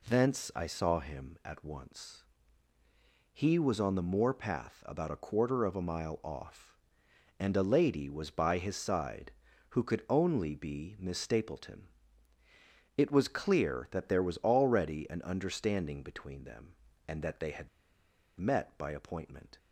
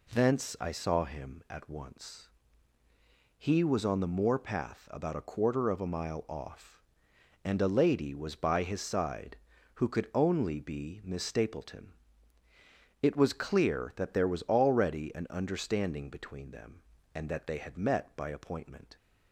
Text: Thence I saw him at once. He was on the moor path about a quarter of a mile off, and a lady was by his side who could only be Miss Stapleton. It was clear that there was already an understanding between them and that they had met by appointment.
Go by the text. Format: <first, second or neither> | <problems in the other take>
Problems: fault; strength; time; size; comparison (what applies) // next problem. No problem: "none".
second | pauses between "had" and "met"; noticeable; at 17.6 s; 0.70 s long